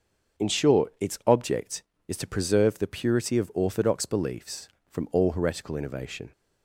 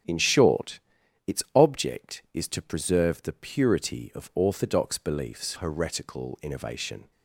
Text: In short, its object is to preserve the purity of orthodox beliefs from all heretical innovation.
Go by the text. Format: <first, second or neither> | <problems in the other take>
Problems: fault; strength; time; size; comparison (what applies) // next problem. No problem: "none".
first | starts louder than the rest; strong; until 1.6 s; 9.5 dB; also in the first // skips "from all"; at 5.5 s